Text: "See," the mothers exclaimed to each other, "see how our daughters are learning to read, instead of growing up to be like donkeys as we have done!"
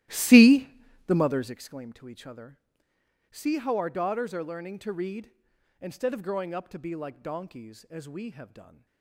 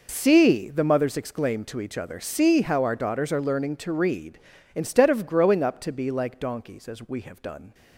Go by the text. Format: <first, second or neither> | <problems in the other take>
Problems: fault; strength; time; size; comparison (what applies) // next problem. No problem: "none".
second | starts louder than the rest; strong; until 1.6 s; 15 dB